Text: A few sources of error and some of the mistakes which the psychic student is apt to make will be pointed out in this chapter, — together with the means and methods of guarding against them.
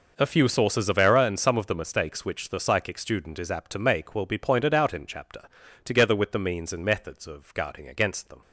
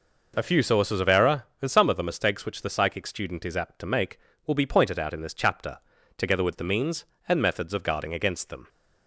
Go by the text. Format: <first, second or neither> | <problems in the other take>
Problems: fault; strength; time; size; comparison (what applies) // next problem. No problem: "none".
second | skips "this"; at 5.0 s